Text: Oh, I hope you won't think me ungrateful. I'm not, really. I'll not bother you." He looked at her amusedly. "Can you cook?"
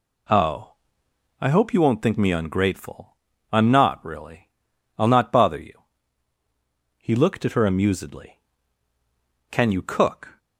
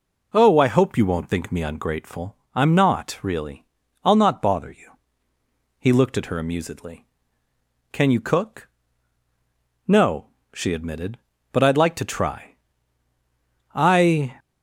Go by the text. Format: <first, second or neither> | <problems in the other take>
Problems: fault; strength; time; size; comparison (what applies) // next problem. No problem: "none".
first | goes on to say "No she admitted but I'd like to try I"; strong; from 9.8 s on; 4.5 s long